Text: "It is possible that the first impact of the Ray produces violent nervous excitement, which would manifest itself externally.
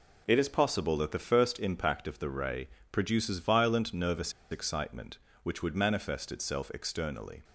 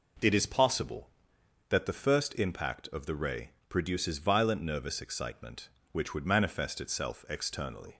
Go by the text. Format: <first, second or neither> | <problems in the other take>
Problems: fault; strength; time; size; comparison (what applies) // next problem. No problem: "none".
second | pauses between "Ray" and "produces"; slight; at 2.6 s; 0.22 s long; slight in the second // pauses between "nervous" and "excitement"; slight; at 4.3 s; 0.19 s long